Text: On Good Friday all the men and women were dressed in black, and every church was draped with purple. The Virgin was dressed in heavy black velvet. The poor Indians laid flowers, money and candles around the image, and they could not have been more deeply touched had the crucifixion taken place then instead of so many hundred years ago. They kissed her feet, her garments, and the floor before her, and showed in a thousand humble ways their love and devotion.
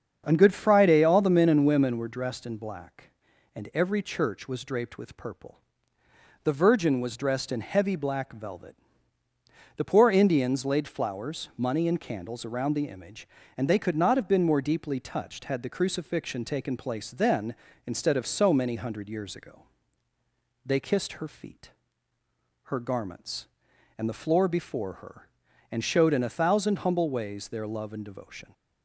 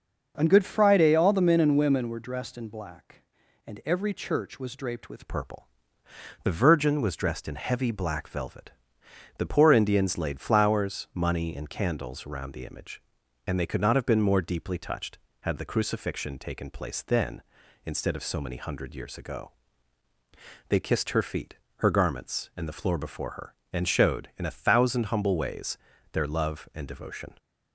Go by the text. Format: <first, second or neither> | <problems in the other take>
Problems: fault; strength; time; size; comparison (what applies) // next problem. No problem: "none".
first | starts louder than the rest; noticeable; until 1.3 s; 6 dB; strong in the first // changes voice at "purple"; from 5.2 s on; 22.1 s long // pauses between "ways" and "their"; slight; at 25.7 s; 0.34 s long